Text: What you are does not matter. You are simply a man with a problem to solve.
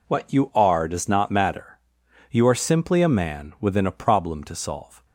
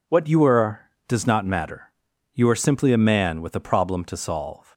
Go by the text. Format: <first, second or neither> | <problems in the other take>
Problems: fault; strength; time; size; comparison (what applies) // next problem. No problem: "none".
second | says "within" for "with"; at 3.5 s